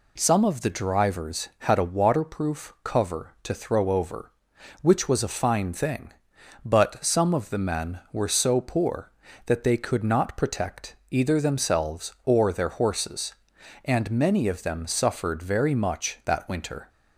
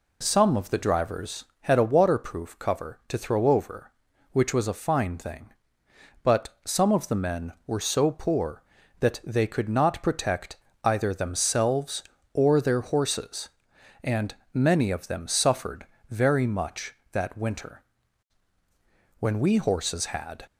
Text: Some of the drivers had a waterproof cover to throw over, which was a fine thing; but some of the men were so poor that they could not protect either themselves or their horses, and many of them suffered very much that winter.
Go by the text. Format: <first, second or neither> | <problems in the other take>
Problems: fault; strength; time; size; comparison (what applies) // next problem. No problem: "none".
first | pauses between "protect" and "either"; slight; at 10.5 s; 0.26 s long; slight in the first // pauses between "and" and "many"; slight; at 14.3 s; 0.18 s long // pauses between "suffered" and "very"; slight; at 15.8 s; 0.24 s long // goes on to say "When we horses had"; noticeable; from 19.1 s on; 1.2 s long